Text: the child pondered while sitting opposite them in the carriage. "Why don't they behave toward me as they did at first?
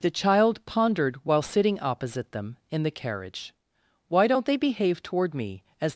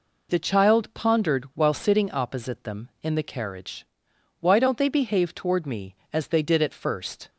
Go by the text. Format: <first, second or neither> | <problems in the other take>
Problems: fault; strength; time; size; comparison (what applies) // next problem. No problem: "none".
second | stops before "they did at first"; at 5.9 s